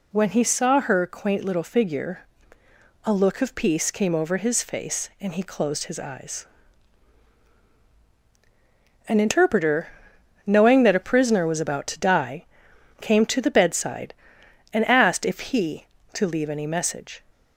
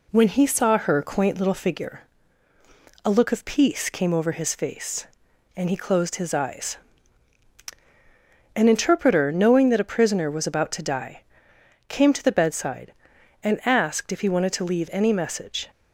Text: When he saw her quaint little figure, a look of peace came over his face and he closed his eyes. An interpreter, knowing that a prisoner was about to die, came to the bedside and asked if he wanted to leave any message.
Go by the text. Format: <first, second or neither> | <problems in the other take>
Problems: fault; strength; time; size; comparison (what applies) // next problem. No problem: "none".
second | skips "wanted"; at 15.9 s